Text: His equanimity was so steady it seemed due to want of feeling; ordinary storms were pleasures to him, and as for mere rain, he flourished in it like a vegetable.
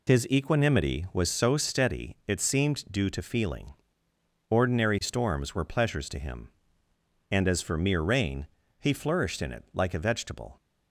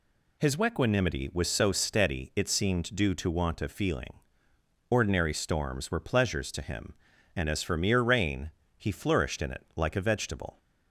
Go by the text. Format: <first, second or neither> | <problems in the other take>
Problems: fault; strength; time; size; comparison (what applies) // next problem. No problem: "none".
second | skips "want of"; at 3.2 s